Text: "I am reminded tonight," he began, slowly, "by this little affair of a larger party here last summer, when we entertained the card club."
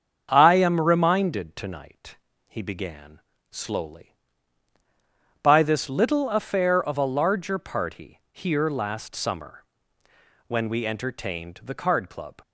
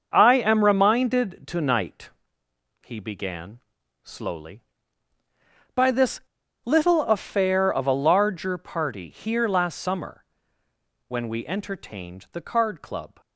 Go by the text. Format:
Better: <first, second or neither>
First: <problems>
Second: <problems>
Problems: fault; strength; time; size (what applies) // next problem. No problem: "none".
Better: first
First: starts louder than the rest; strong; until 1.3 s; 7 dB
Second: starts louder than the rest; until 1.1 s; 6 dB // pauses between "this" and "little"; at 6.2 s; 0.43 s long